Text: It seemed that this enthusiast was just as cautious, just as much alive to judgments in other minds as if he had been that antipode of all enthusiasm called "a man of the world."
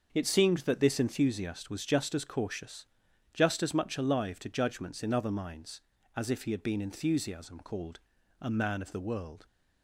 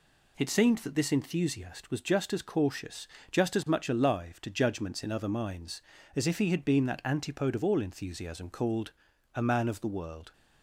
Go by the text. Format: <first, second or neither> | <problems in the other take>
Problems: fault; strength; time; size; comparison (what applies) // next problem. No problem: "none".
second | starts louder than the rest; until 1.1 s; 6.5 dB // skips "that antipode of all"; at 6.8 s // pauses between "called" and "a"; at 7.9 s; 0.42 s long; also in the second